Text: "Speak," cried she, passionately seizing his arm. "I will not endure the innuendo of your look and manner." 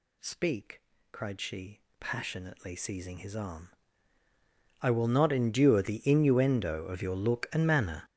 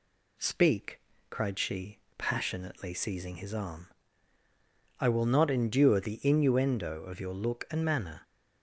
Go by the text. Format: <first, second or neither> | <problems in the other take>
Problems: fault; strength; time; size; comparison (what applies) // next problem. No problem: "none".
second | gets louder; strong; throughout; 15.5 dB